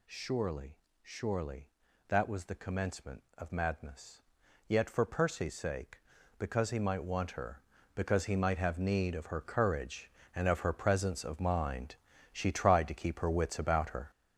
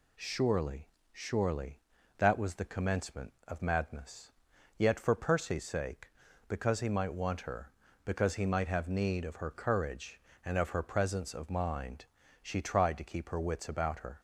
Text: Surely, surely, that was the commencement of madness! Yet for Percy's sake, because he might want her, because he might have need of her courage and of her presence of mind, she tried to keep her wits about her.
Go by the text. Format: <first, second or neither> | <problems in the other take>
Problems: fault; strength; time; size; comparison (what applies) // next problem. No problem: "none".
second | gets louder; strong; throughout; 7.5 dB